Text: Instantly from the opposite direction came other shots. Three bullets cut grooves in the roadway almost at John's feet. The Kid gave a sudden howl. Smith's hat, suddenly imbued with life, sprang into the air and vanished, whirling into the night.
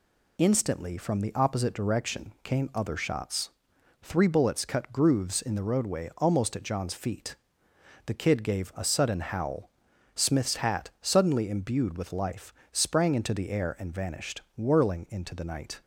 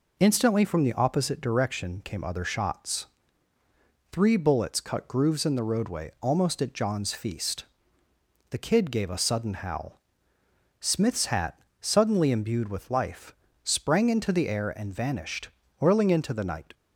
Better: first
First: none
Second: says "feast" for "feet"; at 7.1 s

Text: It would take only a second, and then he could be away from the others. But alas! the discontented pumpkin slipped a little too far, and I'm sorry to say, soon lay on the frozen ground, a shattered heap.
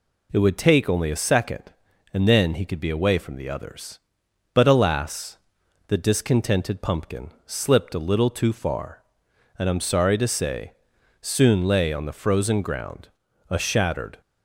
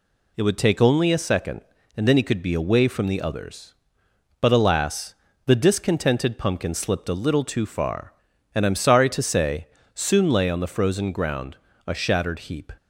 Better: second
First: pauses between "pumpkin" and "slipped"; slight; at 7.3 s; 0.16 s long // stops before "heap"; at 14.2 s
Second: none

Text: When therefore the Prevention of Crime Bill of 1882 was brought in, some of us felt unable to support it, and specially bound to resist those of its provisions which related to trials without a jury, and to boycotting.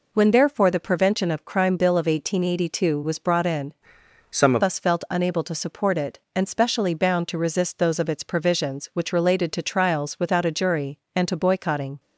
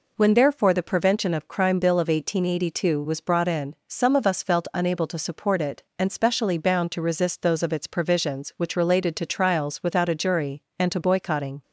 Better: second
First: changes voice from "some" to "of"; from 4.3 to 4.6 s; 0.3 s long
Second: none

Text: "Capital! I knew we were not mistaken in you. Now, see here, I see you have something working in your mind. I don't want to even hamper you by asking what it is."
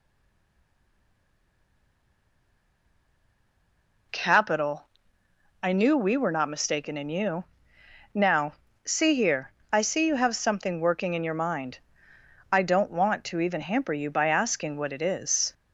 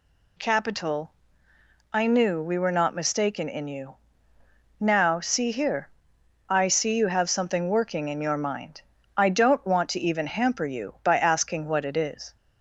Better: second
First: stays silent before the first word; strong; until 4.1 s; 4.1 s long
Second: none

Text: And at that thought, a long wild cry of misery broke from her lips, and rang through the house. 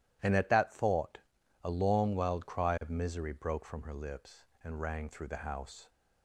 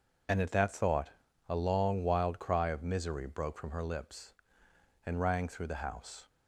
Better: neither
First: none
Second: none

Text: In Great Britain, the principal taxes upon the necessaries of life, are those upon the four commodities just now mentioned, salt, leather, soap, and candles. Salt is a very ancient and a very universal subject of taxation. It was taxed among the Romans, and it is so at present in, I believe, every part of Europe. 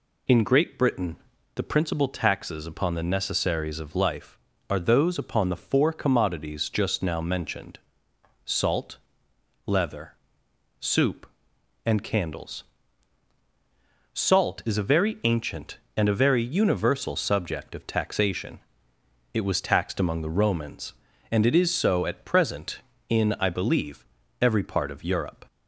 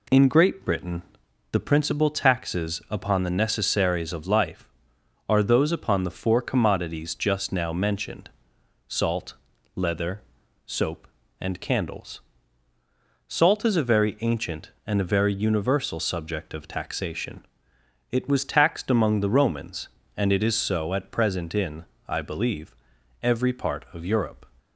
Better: second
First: says "soup" for "soap"; at 10.7 s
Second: none

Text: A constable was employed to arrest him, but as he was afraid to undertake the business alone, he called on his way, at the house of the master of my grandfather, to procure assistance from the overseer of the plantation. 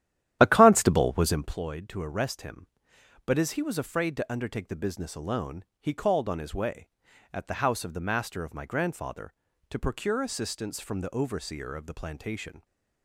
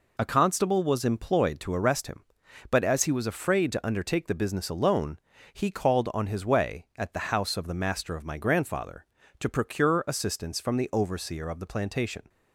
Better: second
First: starts louder than the rest; strong; until 1.6 s; 12 dB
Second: none

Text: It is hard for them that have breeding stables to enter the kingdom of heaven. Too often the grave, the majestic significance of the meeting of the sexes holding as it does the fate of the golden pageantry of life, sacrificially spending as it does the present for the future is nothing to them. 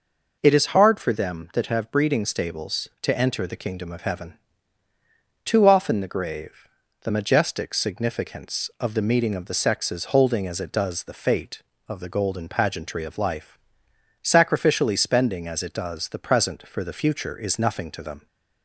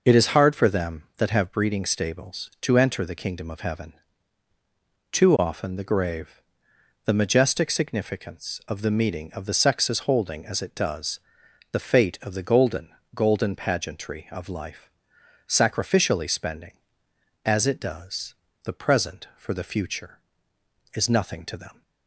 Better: first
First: none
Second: pauses between "does" and "the"; noticeable; at 11.1 s; 0.50 s long // says "golden" twice; at 13.1 s // pauses between "does" and "the"; slight; at 18.3 s; 0.30 s long

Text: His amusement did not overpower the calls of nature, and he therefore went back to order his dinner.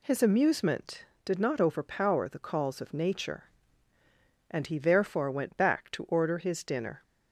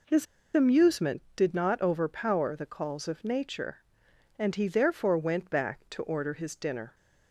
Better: first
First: none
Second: pauses between "His" and "amusement"; slight; at 0.2 s; 0.29 s long

